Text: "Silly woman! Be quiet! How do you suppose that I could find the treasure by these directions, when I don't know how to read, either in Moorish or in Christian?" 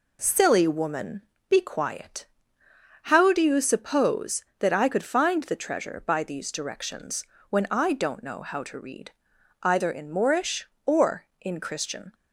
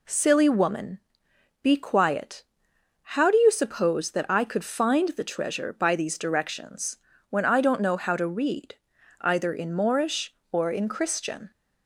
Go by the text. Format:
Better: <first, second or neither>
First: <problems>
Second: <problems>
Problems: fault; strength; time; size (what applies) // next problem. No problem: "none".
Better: neither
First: none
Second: none